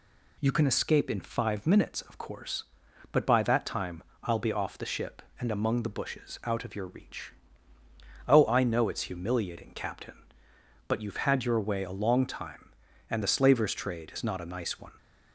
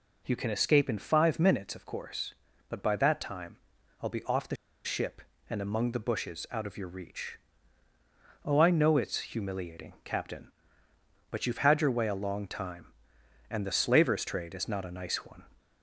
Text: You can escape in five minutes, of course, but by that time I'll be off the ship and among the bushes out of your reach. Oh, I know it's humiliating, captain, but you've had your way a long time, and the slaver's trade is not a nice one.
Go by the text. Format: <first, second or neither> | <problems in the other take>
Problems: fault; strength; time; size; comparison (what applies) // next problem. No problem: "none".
first | pauses between "time" and "I'll"; at 3.5 s; 0.44 s long; slight in the first // pauses between "the" and "ship"; slight; at 4.5 s; 0.29 s long